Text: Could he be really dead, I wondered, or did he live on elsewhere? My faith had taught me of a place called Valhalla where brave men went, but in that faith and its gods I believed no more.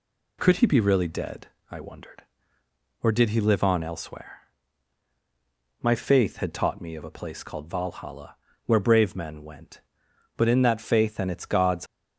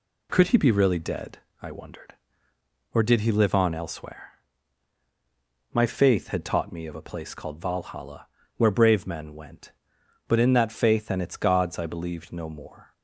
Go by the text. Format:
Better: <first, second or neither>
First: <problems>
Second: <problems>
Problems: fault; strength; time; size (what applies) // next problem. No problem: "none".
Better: second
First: pauses between "Valhalla" and "where"; slight; at 8.3 s; 0.30 s long // stops before "I believed no more"; at 11.8 s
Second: pauses between "Valhalla" and "where"; slight; at 8.2 s; 0.30 s long